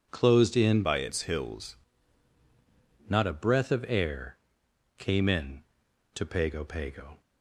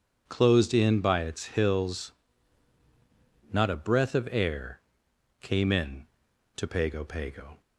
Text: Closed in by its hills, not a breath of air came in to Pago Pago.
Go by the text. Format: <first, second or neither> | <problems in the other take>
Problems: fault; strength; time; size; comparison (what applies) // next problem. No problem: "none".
second | changes voice from "by" to "hills"; from 0.8 to 1.7 s; 0.9 s long // pauses between "air" and "came"; noticeable; at 4.3 s; 0.62 s long; noticeable in the second